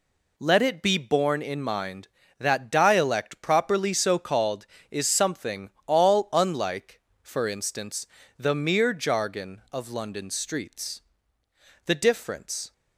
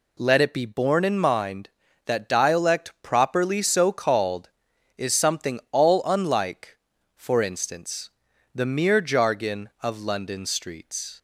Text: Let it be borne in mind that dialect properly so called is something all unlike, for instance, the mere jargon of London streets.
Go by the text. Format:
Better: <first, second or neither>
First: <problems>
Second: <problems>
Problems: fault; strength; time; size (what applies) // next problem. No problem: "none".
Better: second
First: pauses between "something" and "all"; slight; at 5.7 s; 0.16 s long // goes on to say "The difference"; noticeable; from 11.8 s on; 0.88 s long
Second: none